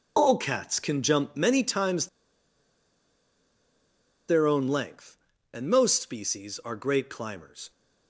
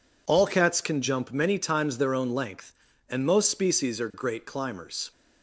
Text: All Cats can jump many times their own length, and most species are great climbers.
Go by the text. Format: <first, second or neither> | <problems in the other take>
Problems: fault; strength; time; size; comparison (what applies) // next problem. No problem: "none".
second | pauses between "times" and "their"; strong; at 2.0 s; 2.2 s long